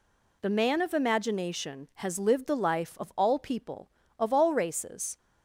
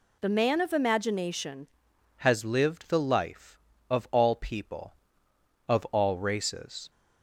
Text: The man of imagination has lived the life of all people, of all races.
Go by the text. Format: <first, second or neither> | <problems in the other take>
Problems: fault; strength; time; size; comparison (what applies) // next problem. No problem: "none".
first | changes voice at "has"; from 2.1 s on; 4.8 s long